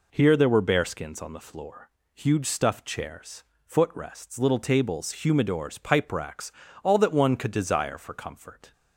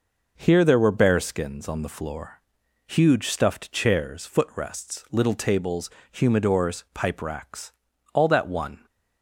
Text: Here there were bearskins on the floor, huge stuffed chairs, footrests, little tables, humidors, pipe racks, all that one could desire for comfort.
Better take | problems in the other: first | stops before "could desire for comfort"; at 8.8 s

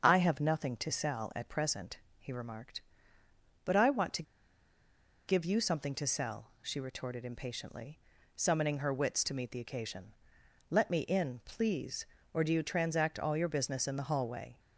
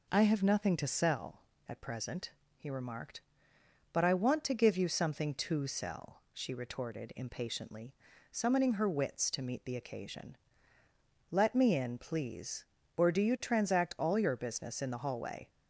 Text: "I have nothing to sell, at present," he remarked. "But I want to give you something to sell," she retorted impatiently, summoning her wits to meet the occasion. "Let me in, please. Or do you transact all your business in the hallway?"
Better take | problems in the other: second | starts louder than the rest; until 1.0 s; 6.5 dB // pauses between "to" and "give"; at 4.2 s; 1.0 s long

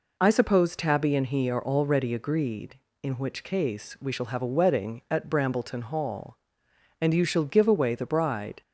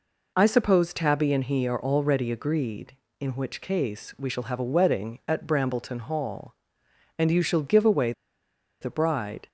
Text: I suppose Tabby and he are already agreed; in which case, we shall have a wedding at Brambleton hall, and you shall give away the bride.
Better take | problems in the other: first | pauses between "away" and "the"; noticeable; at 8.1 s; 0.68 s long

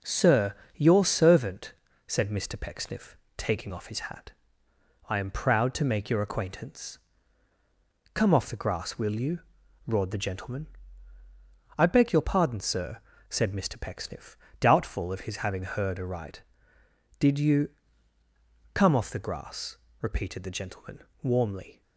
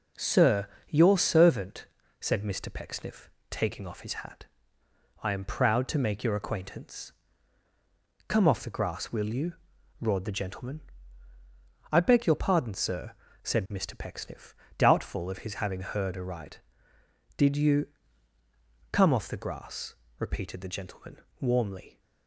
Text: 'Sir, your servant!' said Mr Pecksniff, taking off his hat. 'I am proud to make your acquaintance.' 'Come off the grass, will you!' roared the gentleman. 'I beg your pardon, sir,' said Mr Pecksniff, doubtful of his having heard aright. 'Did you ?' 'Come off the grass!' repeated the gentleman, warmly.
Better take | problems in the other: neither | none

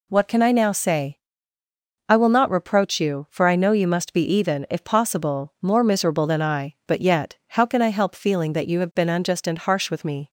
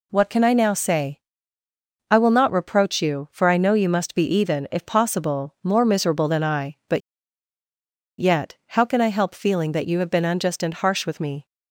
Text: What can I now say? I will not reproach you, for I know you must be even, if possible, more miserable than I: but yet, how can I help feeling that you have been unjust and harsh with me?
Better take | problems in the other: first | pauses between "but" and "yet"; at 7.0 s; 1.2 s long

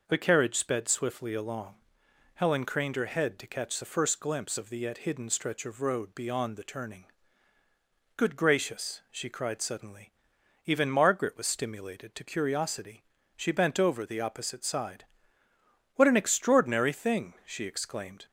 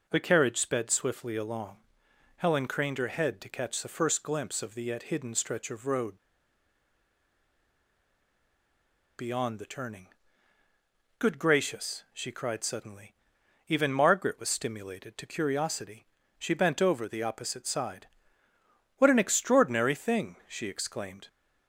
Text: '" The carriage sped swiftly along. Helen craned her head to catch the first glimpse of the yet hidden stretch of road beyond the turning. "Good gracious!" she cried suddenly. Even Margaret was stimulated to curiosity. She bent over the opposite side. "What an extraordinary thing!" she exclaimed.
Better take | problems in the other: first | pauses between "road" and "beyond"; strong; at 6.1 s; 2.9 s long

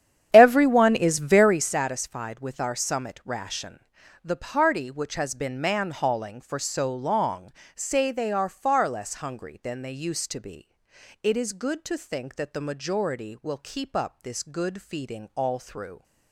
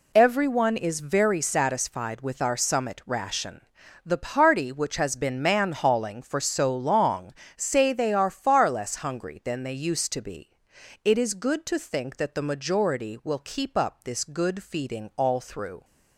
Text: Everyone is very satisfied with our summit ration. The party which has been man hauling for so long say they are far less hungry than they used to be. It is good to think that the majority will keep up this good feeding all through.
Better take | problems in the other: second | starts louder than the rest; strong; until 1.8 s; 9.5 dB // pauses between "long" and "say"; slight; at 7.5 s; 0.24 s long; slight in the second

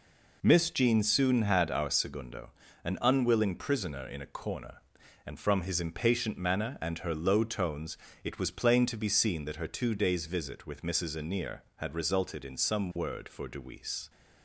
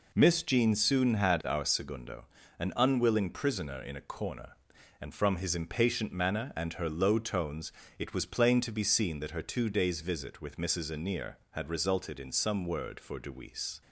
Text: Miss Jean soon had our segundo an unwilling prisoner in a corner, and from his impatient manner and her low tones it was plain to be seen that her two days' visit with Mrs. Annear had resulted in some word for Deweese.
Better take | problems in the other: neither | pauses between "segundo" and "an"; slight; the same in both // pauses between "tones" and "it"; slight; the same in both

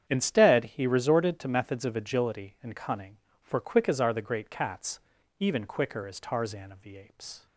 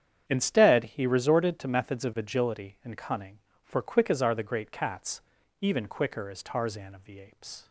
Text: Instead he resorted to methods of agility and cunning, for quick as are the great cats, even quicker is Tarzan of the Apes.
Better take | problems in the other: neither | starts louder than the rest; strong; the same in both

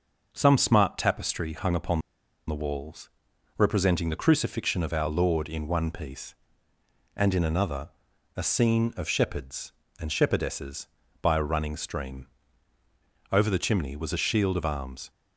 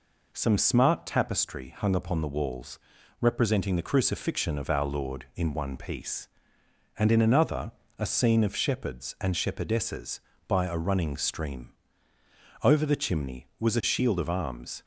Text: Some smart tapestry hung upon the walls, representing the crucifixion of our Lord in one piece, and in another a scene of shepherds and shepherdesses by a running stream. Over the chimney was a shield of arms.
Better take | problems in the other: second | starts louder than the rest; until 1.3 s; 6 dB // pauses between "upon" and "the"; noticeable; at 2.0 s; 0.47 s long // pauses between "another" and "a"; noticeable; at 7.9 s; 0.46 s long; slight in the second

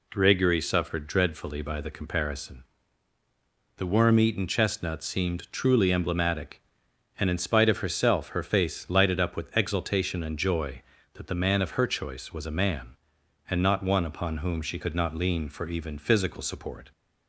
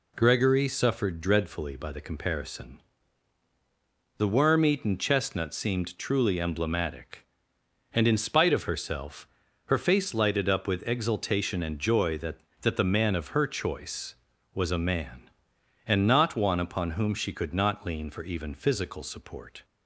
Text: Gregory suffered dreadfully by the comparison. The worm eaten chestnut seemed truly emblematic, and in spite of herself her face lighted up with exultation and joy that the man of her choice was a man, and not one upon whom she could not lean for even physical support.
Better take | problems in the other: first | pauses between "herself" and "her"; at 9.2 s; 0.38 s long // says "that" twice; at 12.6 s

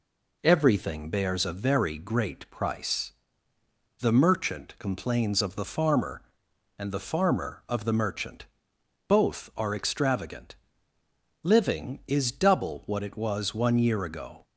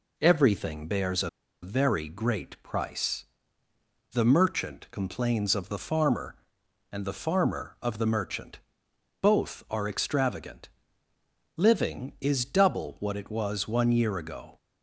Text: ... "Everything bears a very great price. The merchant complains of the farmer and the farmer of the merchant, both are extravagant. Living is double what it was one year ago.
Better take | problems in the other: first | pauses between "a" and "very"; slight; at 1.2 s; 0.33 s long

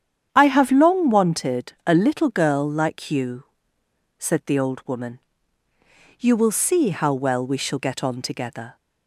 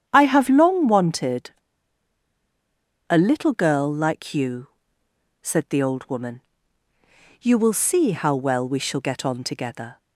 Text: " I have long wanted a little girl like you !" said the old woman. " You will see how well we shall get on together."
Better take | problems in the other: first | starts louder than the rest; strong; until 1.0 s; 9.5 dB; strong in the first // pauses between "wanted" and "a"; strong; at 1.5 s; 1.5 s long

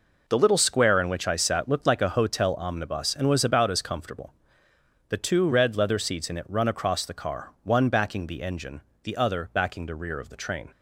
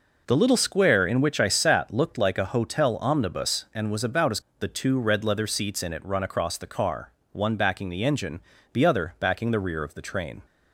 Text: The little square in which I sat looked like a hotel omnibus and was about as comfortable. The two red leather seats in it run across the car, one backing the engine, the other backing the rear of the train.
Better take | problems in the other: first | skips "comfortable"; at 4.4 s

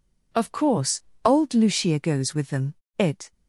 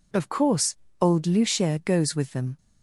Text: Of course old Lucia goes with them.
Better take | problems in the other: second | pauses between "course" and "old"; slight; at 1.0 s; 0.22 s long; slight in the second // goes on to say "It"; slight; from 2.9 s on; 0.34 s long

